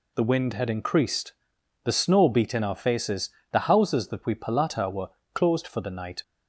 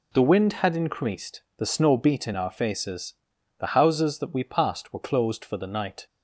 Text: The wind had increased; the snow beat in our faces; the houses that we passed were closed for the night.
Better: second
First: says "palata" for "passed"; at 4.3 s // pauses between "were" and "closed"; slight; at 5.1 s; 0.24 s long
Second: none

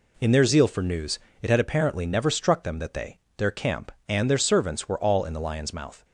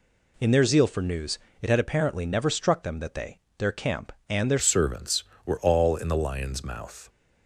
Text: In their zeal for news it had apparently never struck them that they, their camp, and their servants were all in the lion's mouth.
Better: first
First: pauses between "news" and "it"; slight; at 1.1 s; 0.22 s long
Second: pauses between "news" and "it"; slight; at 1.3 s; 0.22 s long // changes voice at "servants"; from 4.6 s on; 2.4 s long

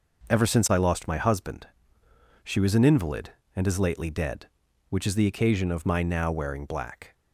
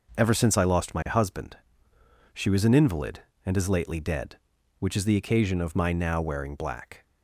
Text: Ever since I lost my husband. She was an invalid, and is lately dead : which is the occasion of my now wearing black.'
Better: neither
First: starts louder than the rest; noticeable; until 1.3 s; 6 dB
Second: starts louder than the rest; until 1.2 s; 6 dB

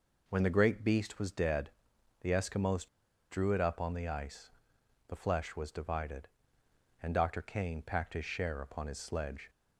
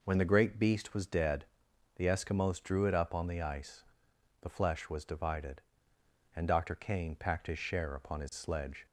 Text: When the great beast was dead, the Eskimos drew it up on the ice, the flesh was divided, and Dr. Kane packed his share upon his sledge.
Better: second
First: pauses between "Eskimos" and "drew"; at 2.8 s; 0.42 s long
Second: none

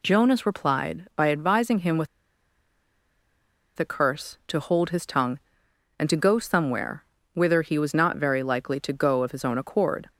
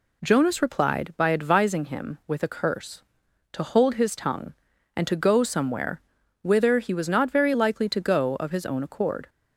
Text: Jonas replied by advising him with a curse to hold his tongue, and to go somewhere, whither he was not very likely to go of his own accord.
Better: second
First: pauses between "with" and "a"; strong; at 2.0 s; 1.7 s long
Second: none

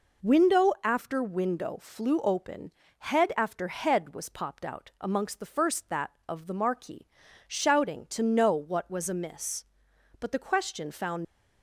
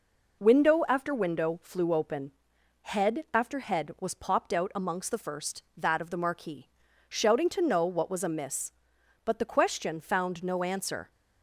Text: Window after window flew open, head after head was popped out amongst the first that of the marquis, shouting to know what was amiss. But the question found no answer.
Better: second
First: stops before "no answer"; at 11.2 s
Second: none

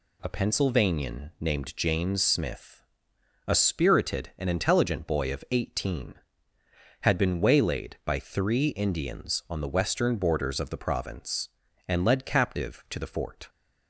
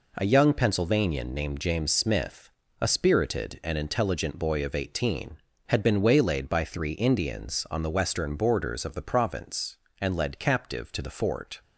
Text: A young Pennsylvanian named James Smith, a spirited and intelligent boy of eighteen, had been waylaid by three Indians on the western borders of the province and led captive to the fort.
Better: second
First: skips "young"; at 0.2 s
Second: none

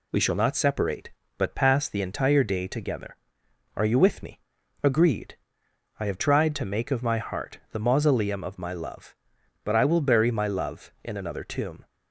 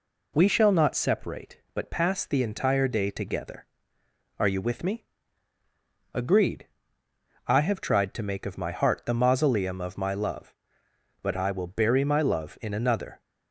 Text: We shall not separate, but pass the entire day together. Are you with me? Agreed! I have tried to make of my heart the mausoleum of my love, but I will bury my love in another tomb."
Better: first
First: none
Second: stops before "tomb"; at 13.2 s

